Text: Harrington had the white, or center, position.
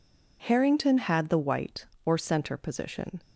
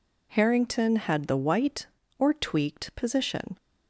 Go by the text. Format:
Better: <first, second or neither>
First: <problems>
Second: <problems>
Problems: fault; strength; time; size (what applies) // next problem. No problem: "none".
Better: first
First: none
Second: says "tweaked" for "center"; at 2.3 s